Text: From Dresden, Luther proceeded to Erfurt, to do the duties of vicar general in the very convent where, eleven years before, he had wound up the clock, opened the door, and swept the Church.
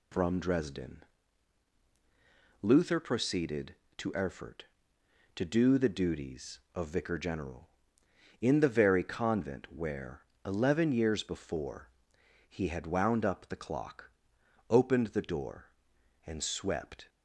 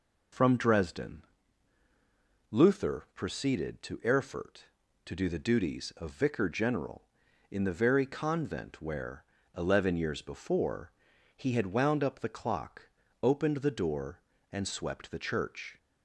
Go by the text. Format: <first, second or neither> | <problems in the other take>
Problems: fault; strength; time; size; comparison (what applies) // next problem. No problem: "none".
second | stops before "the Church"; at 17.0 s